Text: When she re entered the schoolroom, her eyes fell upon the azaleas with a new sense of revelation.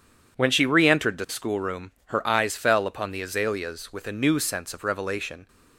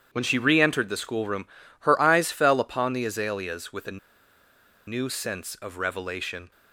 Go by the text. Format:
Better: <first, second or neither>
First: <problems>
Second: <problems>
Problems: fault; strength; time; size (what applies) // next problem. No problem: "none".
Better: first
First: none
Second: starts louder than the rest; strong; until 1.1 s; 9 dB // pauses between "a" and "new"; noticeable; at 3.9 s; 0.88 s long